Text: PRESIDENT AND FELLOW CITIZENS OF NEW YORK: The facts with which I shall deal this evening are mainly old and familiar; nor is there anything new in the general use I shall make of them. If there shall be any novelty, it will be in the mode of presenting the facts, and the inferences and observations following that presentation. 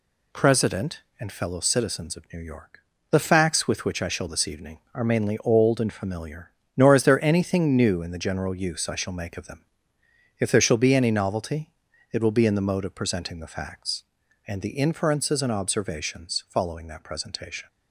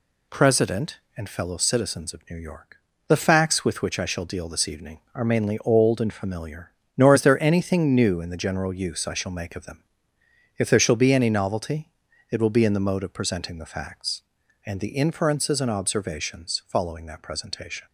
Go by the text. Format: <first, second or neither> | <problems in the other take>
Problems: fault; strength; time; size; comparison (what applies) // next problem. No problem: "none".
second | skips "deal"; at 4.2 s